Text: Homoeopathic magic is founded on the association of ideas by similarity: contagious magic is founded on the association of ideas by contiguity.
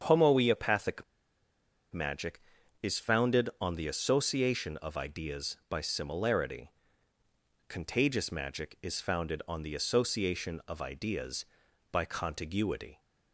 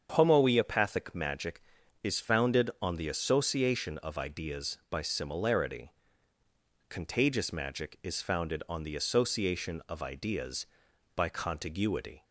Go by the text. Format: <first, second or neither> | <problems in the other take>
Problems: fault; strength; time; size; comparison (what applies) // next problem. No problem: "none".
second | starts louder than the rest; strong; until 1.9 s; 7.5 dB; strong in the second // pauses between "Homoeopathic" and "magic"; noticeable; at 1.0 s; 0.89 s long